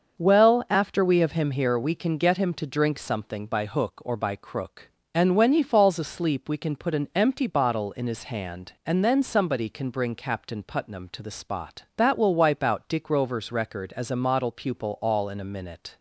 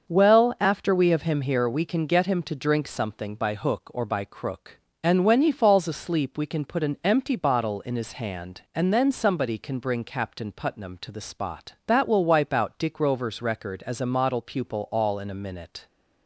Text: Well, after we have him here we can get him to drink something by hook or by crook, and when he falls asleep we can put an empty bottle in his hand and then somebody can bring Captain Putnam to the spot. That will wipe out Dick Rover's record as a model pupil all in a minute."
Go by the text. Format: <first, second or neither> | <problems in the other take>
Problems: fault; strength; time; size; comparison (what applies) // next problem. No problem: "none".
neither | starts louder than the rest; the same in both